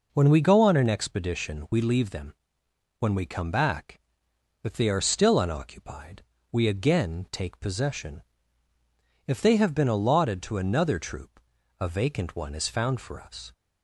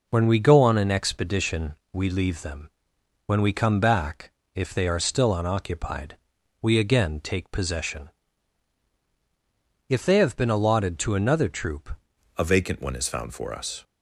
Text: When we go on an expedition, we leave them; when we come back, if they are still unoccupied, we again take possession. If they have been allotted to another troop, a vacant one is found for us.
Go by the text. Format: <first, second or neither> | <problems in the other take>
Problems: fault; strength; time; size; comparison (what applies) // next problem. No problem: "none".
first | changes voice at "a"; from 12.3 s on; 1.5 s long